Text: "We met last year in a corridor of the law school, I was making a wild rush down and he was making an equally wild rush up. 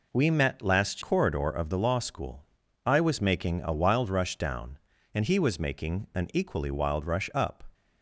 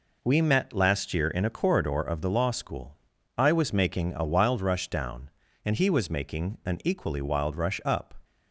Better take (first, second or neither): second